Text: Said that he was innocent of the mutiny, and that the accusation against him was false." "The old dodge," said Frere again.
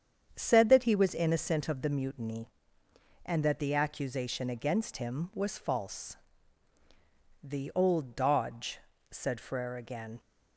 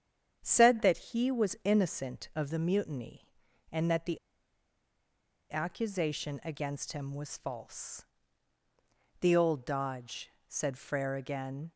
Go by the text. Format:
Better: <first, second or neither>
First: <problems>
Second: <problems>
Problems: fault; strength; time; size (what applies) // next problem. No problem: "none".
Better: first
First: starts louder than the rest; strong; until 1.3 s; 8 dB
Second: starts louder than the rest; strong; until 1.4 s; 8.5 dB // pauses between "the" and "accusation"; strong; at 4.1 s; 1.3 s long